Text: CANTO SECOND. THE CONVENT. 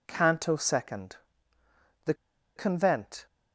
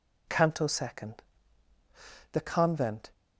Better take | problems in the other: second | pauses between "THE" and "CONVENT"; at 2.1 s; 0.42 s long

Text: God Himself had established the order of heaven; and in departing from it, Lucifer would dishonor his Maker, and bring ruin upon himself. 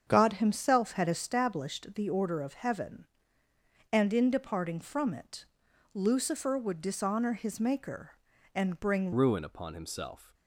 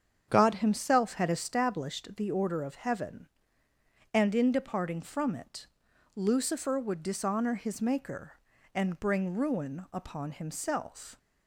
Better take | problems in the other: second | starts louder than the rest; strong; until 1.0 s; 7.5 dB; strong in the second // changes voice at "ruin"; from 9.1 s on; 1.2 s long

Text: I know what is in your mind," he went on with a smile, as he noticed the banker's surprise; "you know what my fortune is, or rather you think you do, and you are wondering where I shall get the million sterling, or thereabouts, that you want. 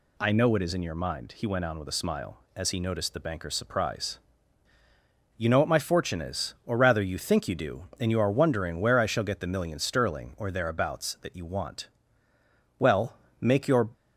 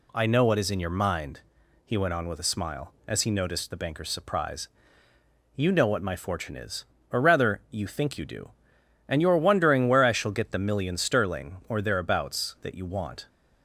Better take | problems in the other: second | goes on to say "Well make your"; noticeable; from 12.7 s on; 1.1 s long

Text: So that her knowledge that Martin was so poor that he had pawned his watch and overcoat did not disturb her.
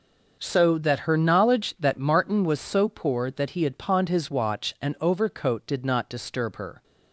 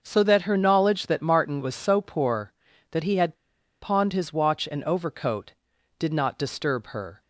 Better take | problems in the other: first | pauses between "had" and "pawned"; noticeable; at 3.3 s; 0.46 s long

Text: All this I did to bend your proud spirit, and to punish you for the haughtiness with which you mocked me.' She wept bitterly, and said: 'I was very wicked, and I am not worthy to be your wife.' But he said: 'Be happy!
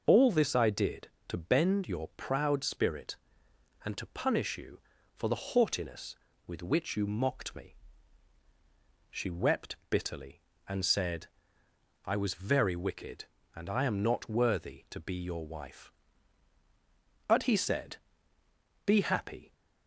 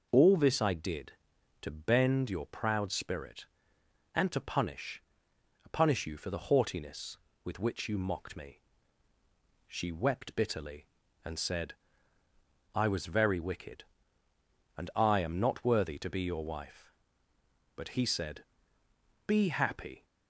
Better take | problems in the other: first | says "punish" twice; at 5.7 s

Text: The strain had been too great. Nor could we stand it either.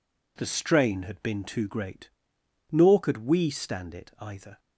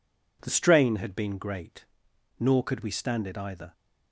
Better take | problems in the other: first | skips "too"; at 1.3 s

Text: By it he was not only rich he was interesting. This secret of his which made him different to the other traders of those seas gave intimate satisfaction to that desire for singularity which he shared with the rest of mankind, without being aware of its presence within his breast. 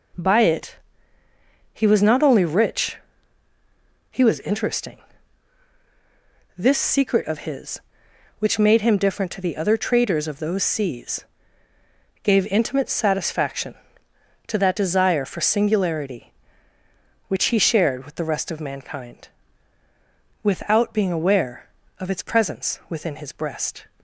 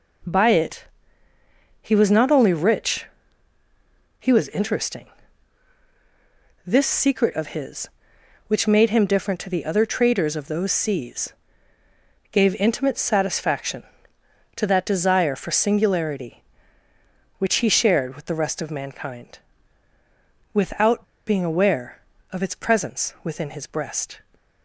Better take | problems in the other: first | pauses between "it" and "he"; noticeable; at 0.8 s; 0.96 s long; noticeable in the first // pauses between "rich" and "he"; at 3.0 s; 1.1 s long; also in the first // pauses between "seas" and "gave"; noticeable; at 11.3 s; 0.98 s long; noticeable in the first // pauses between "without" and "being"; slight; at 21.0 s; 0.23 s long

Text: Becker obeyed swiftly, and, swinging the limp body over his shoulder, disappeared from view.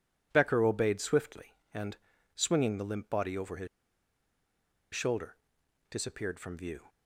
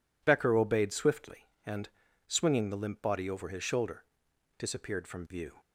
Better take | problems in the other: second | pauses between "his" and "shoulder"; strong; at 3.6 s; 1.2 s long

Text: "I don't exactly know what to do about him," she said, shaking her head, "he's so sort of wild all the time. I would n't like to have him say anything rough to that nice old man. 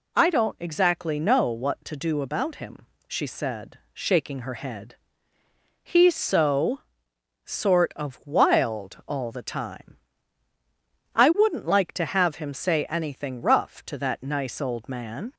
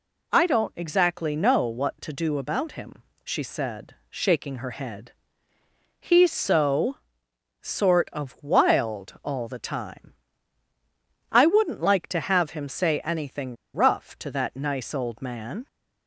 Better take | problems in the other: first | pauses between "so" and "sort"; noticeable; at 6.9 s; 0.66 s long; noticeable in the first // pauses between "anything" and "rough"; slight; at 13.5 s; 0.18 s long

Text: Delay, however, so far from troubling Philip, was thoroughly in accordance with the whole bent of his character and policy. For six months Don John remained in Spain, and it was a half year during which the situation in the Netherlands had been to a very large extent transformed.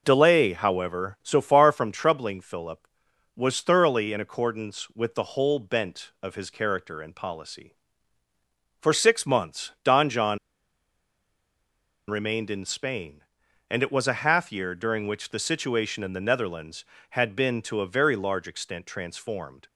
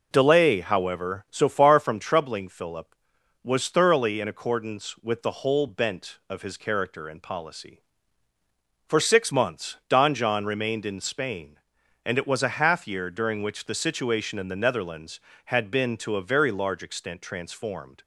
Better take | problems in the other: second | pauses between "John" and "remained"; strong; at 10.3 s; 1.7 s long

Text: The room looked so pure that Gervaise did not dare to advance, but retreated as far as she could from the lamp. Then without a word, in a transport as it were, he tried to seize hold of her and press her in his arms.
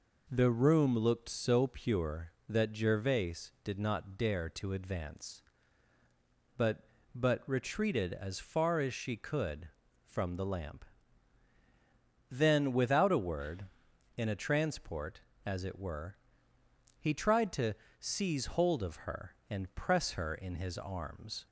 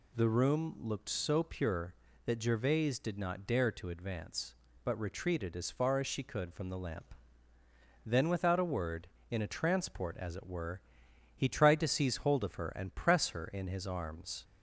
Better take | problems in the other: second | says "but" twice; at 7.1 s // pauses between "to" and "seize"; slight; at 17.7 s; 0.24 s long

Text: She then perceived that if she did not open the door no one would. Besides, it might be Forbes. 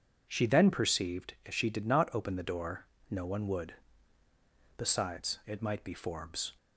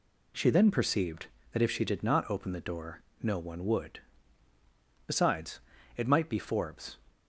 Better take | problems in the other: second | skips "that"; at 1.3 s // pauses between "door" and "no"; slight; at 2.8 s; 0.24 s long; slight in the second

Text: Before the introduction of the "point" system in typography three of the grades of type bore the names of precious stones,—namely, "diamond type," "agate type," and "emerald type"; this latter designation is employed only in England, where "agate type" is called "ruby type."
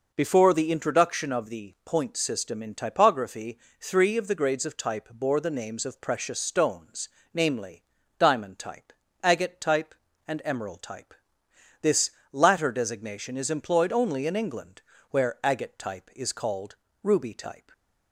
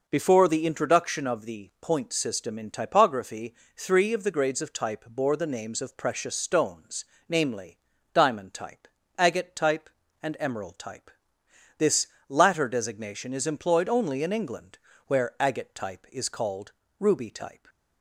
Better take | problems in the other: neither | pauses between "typography" and "three"; slight; the same in both // pauses between "this" and "latter"; slight; the same in both // pauses between "called" and "ruby"; slight; the same in both

